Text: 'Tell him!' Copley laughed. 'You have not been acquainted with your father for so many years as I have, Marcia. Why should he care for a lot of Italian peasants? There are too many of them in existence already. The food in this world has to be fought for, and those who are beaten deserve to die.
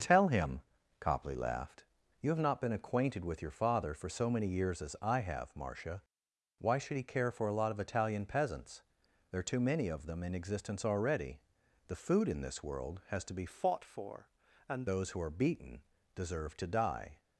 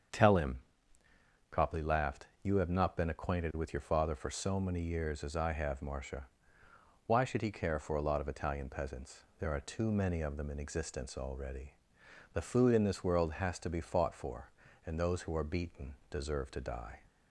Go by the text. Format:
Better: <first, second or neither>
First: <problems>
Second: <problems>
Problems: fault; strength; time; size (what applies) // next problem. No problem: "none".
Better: second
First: starts louder than the rest; until 1.4 s; 6.5 dB // changes voice from "fought" to "and"; from 13.4 to 14.8 s; 1.4 s long // pauses between "beaten" and "deserve"; slight; at 15.8 s; 0.32 s long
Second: starts louder than the rest; strong; until 2.0 s; 7.5 dB // pauses between "beaten" and "deserve"; slight; at 15.9 s; 0.16 s long